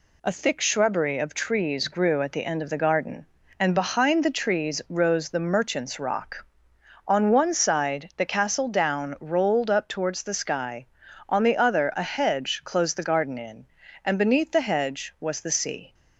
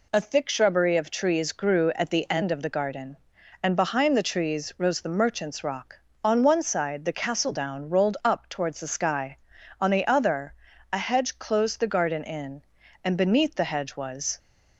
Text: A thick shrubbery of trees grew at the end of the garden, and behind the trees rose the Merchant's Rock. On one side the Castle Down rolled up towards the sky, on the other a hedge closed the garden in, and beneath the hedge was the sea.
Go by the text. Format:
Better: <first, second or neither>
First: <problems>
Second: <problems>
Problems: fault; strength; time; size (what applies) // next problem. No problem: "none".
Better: first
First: none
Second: pauses between "other" and "a"; slight; at 10.5 s; 0.36 s long // stops before "the sea"; at 14.3 s